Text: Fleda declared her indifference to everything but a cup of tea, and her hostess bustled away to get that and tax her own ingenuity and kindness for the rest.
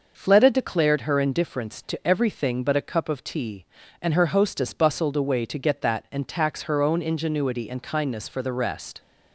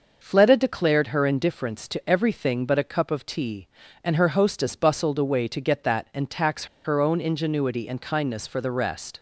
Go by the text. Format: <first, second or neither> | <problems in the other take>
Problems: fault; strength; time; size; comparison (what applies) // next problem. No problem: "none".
first | pauses between "tax" and "her"; slight; at 6.6 s; 0.18 s long